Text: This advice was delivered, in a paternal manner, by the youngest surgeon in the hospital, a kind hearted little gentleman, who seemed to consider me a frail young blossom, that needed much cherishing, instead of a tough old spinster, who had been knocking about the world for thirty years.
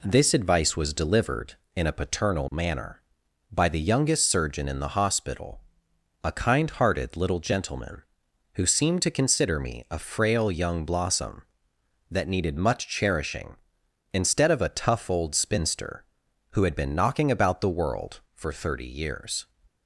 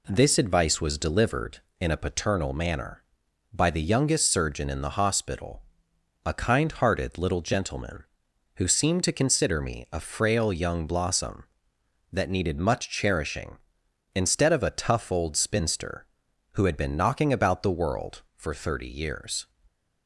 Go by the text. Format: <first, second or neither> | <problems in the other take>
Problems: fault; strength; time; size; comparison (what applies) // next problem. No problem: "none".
neither | none